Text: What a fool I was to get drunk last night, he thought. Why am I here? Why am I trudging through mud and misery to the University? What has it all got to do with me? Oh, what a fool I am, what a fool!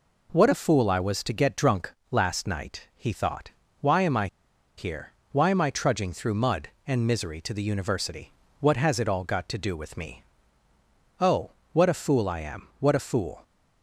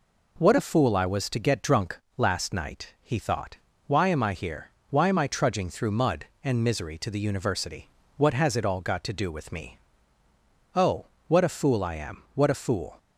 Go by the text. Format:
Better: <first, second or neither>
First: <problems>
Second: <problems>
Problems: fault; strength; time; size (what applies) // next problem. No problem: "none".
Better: second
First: pauses between "drunk" and "last"; slight; at 1.9 s; 0.16 s long // pauses between "I" and "here"; noticeable; at 4.2 s; 0.50 s long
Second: pauses between "drunk" and "last"; slight; at 1.9 s; 0.16 s long